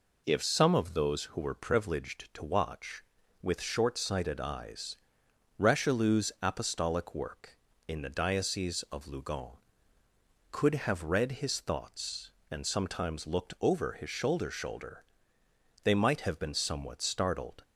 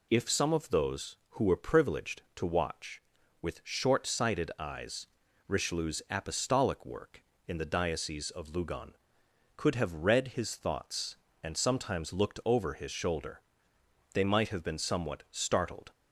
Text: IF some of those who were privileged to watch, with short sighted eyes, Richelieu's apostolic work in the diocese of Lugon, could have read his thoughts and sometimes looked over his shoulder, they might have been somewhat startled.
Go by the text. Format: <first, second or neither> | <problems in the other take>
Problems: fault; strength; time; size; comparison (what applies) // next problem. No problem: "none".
second | says "shoulder" twice; at 14.4 s